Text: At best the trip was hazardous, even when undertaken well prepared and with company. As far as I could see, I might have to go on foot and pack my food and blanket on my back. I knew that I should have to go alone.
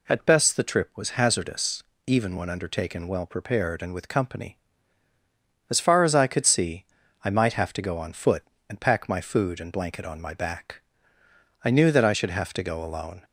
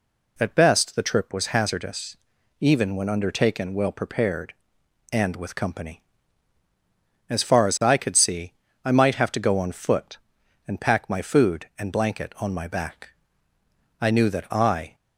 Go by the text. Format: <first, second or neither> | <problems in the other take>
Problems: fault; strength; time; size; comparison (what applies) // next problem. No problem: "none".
first | stops before "should have to go alone"; at 14.9 s